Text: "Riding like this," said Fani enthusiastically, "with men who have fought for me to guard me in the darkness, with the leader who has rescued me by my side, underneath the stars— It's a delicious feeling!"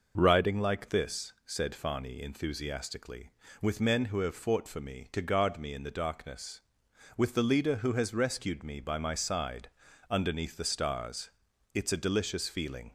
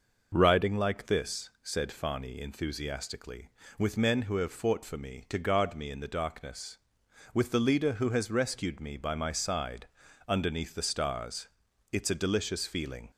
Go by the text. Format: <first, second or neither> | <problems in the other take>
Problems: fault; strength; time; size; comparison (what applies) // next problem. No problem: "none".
neither | none